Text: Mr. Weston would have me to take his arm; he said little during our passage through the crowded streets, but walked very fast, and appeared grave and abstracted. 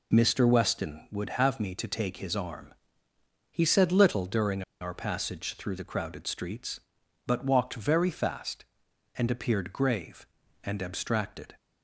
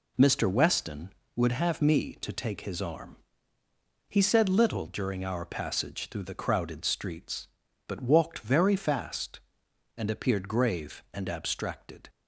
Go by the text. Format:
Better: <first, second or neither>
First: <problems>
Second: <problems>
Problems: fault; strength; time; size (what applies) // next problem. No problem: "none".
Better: second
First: pauses between "during" and "our"; slight; at 4.6 s; 0.19 s long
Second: none